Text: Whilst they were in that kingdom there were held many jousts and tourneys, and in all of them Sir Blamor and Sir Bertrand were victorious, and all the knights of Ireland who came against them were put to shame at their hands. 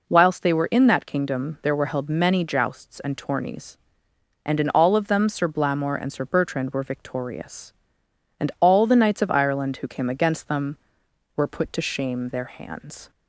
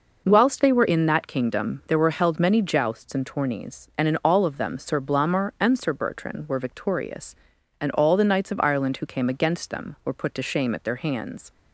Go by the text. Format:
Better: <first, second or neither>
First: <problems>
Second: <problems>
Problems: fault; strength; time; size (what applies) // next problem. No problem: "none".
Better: second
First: skips "at"; at 12.2 s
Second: none